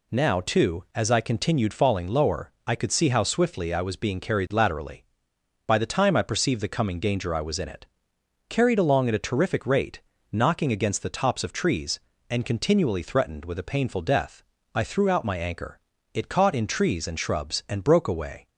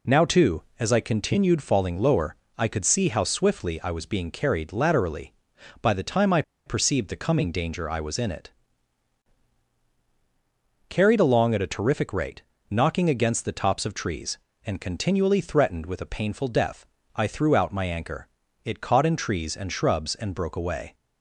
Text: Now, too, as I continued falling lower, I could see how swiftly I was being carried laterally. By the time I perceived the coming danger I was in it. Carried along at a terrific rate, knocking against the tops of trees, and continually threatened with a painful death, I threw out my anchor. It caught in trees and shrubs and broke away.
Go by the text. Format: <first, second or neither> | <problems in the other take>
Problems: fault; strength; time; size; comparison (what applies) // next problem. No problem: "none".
first | pauses between "I" and "perceived"; slight; at 6.4 s; 0.24 s long